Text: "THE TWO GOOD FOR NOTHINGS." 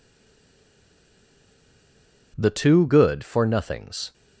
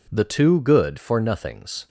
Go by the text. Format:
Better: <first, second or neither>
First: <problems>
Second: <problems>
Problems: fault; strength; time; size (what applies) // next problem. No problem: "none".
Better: second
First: stays silent before the first word; until 2.3 s; 2.3 s long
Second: none